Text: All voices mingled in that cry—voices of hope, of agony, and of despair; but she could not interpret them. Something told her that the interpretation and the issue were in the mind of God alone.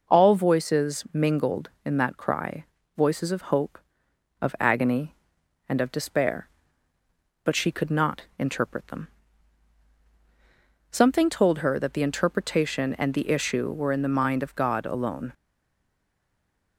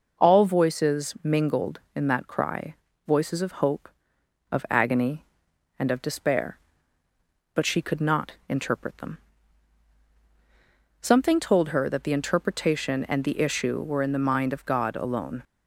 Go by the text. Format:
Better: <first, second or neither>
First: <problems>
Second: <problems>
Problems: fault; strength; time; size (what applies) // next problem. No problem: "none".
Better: second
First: pauses between "not" and "interpret"; slight; at 8.2 s; 0.16 s long // stays silent after the last word; noticeable; from 15.3 s on; 1.4 s long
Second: pauses between "not" and "interpret"; slight; at 8.3 s; 0.16 s long